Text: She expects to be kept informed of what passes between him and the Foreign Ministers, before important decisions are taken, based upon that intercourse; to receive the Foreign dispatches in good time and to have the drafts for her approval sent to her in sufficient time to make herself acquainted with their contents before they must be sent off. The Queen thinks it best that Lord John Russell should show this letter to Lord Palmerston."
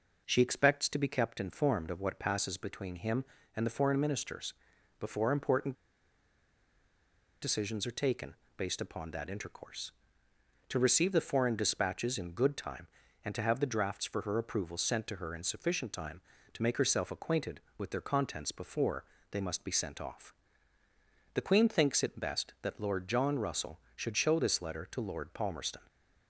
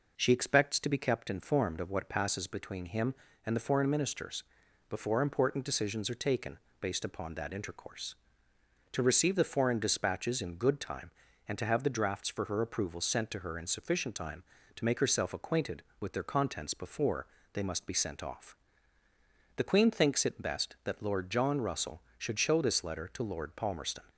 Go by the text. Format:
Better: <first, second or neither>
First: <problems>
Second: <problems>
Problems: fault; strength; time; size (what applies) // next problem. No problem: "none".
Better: second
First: pauses between "important" and "decisions"; strong; at 5.7 s; 1.6 s long // pauses between "before" and "they"; slight; at 19.0 s; 0.28 s long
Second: pauses between "before" and "they"; slight; at 17.2 s; 0.28 s long